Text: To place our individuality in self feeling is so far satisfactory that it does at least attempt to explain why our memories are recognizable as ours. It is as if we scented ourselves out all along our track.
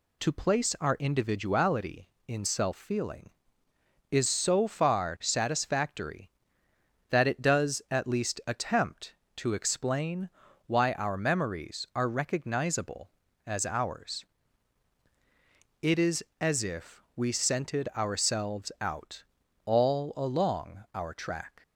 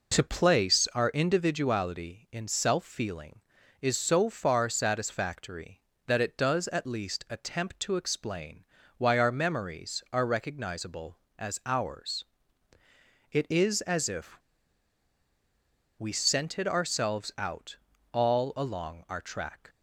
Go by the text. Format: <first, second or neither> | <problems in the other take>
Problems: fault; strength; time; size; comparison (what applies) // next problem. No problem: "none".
first | pauses between "explain" and "why"; slight; at 8.6 s; 0.34 s long; also in the first // pauses between "if" and "we"; strong; at 14.3 s; 1.6 s long // pauses between "out" and "all"; slight; at 17.7 s; 0.36 s long; also in the first